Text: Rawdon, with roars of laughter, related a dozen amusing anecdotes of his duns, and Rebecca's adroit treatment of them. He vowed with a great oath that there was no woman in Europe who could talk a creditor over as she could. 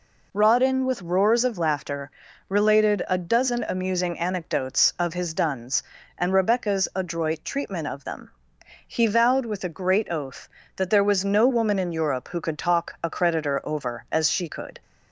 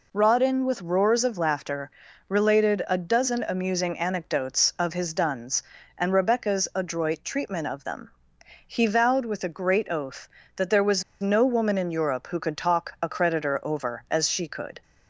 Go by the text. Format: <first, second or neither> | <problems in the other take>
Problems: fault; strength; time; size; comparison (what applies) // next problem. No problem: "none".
first | pauses between "was" and "no"; slight; at 11.0 s; 0.18 s long